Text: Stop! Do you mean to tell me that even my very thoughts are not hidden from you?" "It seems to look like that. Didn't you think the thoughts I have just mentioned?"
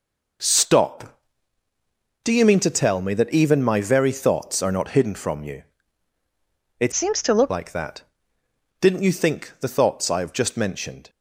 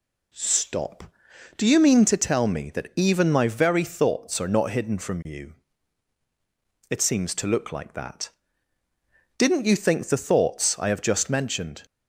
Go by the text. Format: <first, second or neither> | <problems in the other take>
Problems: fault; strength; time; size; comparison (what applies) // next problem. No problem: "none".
second | changes voice from "seems" to "look"; from 6.9 to 7.5 s; 0.6 s long